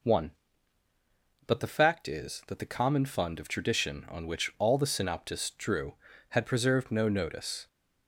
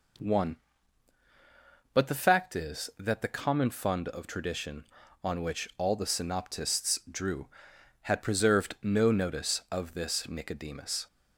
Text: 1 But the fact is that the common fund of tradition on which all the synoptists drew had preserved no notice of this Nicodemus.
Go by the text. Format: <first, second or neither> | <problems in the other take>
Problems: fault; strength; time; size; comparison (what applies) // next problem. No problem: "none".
second | stops before "of this Nicodemus"; at 7.6 s